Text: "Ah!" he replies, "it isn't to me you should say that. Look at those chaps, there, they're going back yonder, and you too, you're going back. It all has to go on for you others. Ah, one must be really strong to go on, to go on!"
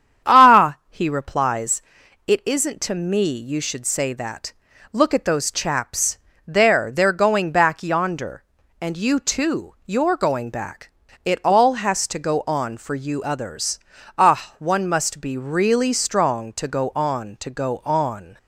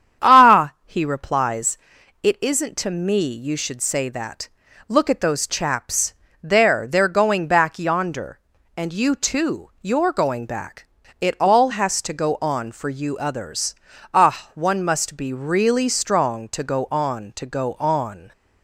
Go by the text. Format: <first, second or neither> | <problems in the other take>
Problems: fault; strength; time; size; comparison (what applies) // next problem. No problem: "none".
neither | starts louder than the rest; strong; the same in both